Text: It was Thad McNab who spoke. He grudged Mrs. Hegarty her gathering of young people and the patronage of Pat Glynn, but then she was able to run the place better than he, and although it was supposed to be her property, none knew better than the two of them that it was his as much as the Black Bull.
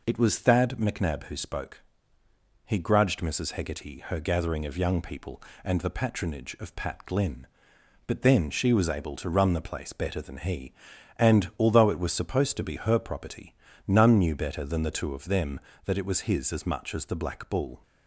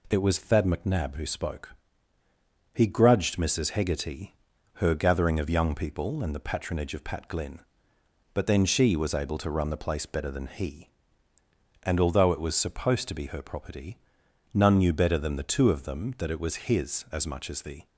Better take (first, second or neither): first